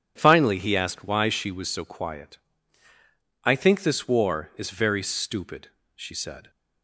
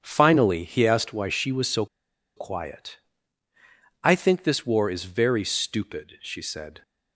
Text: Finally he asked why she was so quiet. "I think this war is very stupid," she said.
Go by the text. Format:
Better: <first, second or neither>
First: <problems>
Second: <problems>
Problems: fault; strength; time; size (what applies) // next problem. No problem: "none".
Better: first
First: none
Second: starts louder than the rest; strong; until 1.0 s; 7.5 dB // pauses between "so" and "quiet"; noticeable; at 1.8 s; 0.50 s long